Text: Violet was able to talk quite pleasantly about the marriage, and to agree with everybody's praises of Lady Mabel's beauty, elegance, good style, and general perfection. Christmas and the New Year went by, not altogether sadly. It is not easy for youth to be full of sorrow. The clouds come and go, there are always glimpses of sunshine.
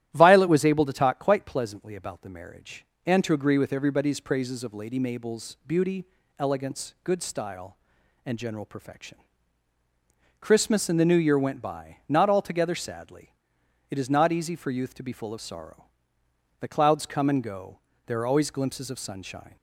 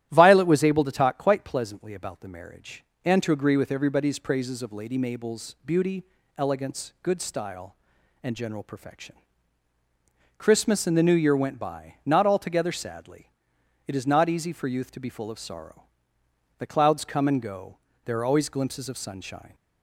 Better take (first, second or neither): neither